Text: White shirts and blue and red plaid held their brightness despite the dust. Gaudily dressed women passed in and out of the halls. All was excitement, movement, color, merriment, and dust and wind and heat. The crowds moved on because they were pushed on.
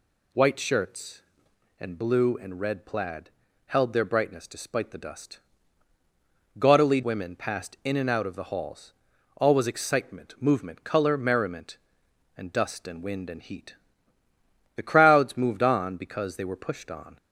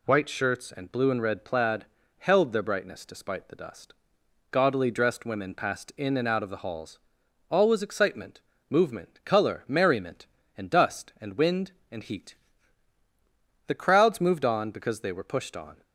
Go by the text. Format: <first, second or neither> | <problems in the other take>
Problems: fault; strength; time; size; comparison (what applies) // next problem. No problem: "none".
second | pauses between "plaid" and "held"; slight; at 3.3 s; 0.36 s long; slight in the second // skips "dressed"; at 7.0 s